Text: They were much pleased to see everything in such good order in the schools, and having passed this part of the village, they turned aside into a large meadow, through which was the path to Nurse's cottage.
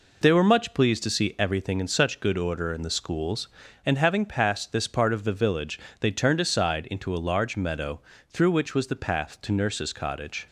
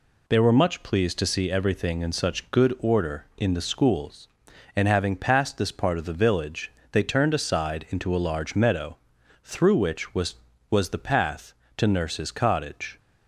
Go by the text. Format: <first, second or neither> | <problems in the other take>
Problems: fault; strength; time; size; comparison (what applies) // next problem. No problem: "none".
first | says "was" twice; at 10.6 s